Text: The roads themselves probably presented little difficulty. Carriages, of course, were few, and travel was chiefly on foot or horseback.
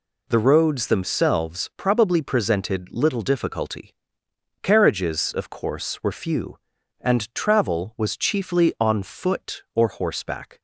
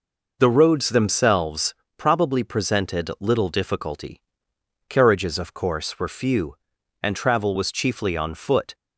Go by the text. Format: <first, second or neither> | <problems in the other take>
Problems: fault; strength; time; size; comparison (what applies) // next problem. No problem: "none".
first | pauses between "themselves" and "probably"; slight; at 1.7 s; 0.22 s long // stops before "or horseback"; at 8.7 s